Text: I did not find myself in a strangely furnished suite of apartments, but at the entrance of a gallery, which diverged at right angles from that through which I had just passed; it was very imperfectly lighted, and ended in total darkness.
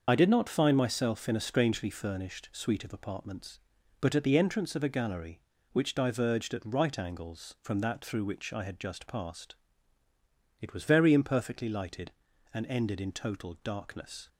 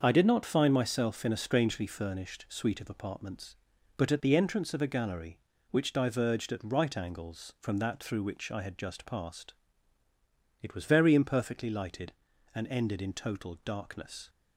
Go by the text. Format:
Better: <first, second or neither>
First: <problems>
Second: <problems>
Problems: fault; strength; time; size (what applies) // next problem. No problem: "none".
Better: second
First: loses the start of "I"; at 0.0 s; 40 ms // starts louder than the rest; until 1.0 s; 6.5 dB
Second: starts louder than the rest; until 1.0 s; 6.5 dB